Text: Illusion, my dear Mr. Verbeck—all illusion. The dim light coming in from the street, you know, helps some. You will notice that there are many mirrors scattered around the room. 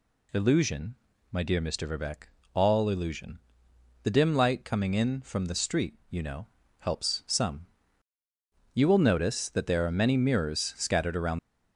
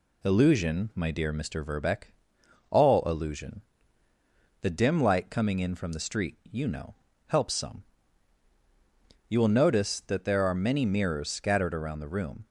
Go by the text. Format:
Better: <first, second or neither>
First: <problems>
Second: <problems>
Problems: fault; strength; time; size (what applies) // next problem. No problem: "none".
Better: second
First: stops before "the room"; at 11.3 s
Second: none